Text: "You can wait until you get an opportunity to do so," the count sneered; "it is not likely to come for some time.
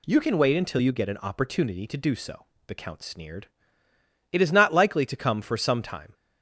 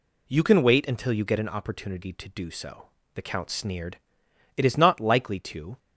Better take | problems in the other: first | stops before "come for some time"; at 5.7 s

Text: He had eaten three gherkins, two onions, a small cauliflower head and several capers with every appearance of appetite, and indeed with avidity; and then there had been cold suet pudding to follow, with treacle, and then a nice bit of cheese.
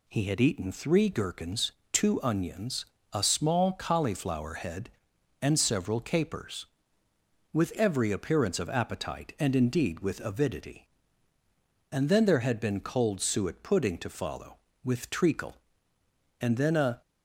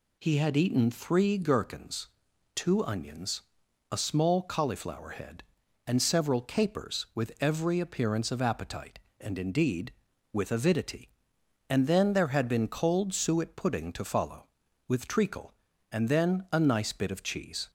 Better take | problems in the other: second | stops before "nice bit of cheese"; at 17.0 s

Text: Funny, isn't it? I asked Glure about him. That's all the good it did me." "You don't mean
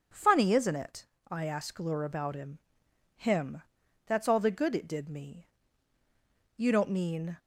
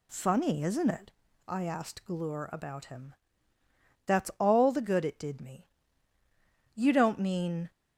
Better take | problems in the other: second | says "him" twice; at 3.1 s

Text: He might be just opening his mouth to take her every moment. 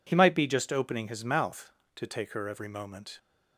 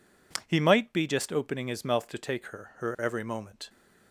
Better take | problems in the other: first | says "her" twice; at 2.7 s

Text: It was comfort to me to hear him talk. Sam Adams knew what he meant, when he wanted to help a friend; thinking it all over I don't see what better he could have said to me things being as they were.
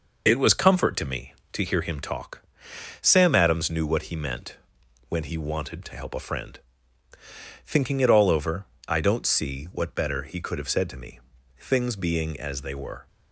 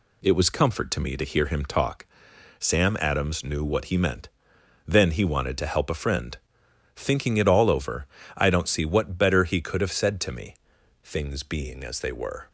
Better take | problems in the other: first | says "then" for "when"; at 4.8 s // pauses between "over" and "I"; slight; at 8.0 s; 0.32 s long; slight in the first // pauses between "me" and "things"; noticeable; at 10.5 s; 0.46 s long; also in the first

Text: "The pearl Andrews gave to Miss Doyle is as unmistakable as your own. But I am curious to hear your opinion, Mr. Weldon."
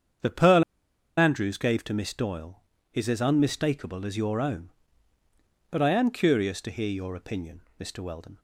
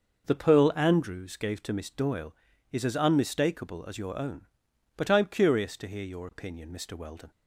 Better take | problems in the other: second | starts louder than the rest; strong; until 1.7 s; 8 dB // pauses between "pearl" and "Andrews"; noticeable; at 0.6 s; 0.56 s long

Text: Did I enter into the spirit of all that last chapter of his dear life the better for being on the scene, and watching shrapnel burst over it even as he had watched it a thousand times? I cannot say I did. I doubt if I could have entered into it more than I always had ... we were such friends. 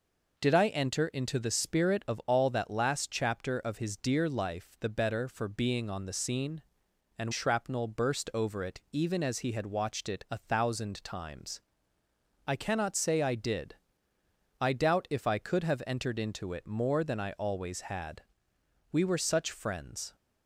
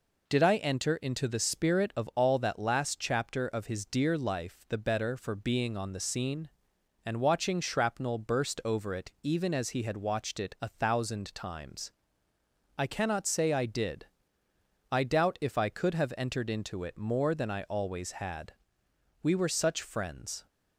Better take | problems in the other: second | skips "watching"; at 7.3 s

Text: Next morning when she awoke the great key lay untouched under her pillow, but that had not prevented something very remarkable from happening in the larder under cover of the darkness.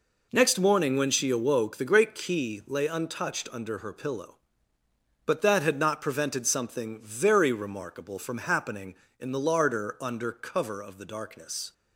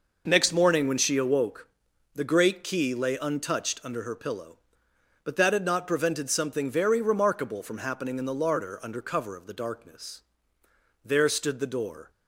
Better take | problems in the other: first | pauses between "awoke" and "the"; noticeable; at 1.6 s; 0.48 s long // goes on to say "There stood the door"; noticeable; from 11.0 s on; 1.0 s long

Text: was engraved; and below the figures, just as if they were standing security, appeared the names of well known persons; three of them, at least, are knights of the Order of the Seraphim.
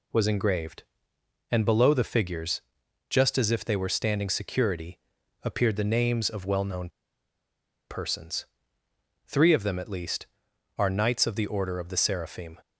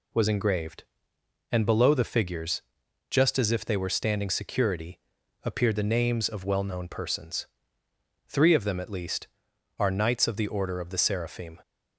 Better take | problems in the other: second | pauses between "known" and "persons"; at 6.8 s; 0.99 s long

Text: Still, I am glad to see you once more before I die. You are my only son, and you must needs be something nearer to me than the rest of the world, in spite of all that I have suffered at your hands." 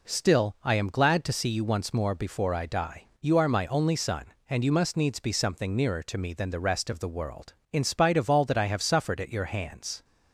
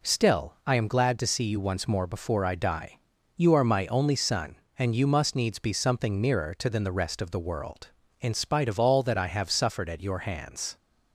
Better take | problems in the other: first | skips "me"; at 6.6 s

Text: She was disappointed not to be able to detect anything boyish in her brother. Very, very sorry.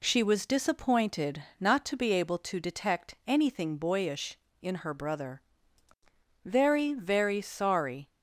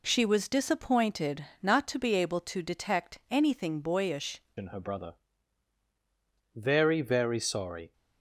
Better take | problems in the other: first | pauses between "disappointed" and "not"; slight; at 1.4 s; 0.16 s long; slight in the first // changes voice at "in"; from 4.5 s on; 3.4 s long

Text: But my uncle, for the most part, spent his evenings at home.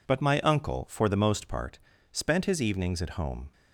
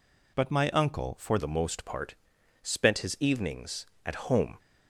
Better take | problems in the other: first | changes voice at "the"; from 1.3 s on; 3.2 s long

